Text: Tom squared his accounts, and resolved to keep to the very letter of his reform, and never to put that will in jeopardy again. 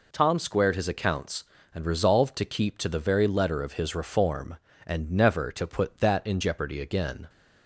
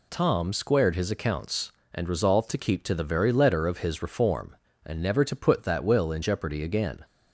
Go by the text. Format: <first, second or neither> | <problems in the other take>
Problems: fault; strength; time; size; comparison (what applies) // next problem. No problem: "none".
second | skips "will"; at 6.2 s